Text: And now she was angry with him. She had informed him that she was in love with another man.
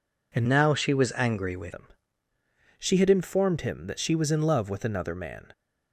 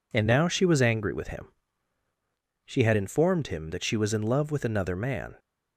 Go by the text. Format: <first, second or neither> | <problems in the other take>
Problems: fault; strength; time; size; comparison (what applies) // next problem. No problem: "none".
second | changes voice from "now" to "with"; from 0.4 to 1.7 s; 1.3 s long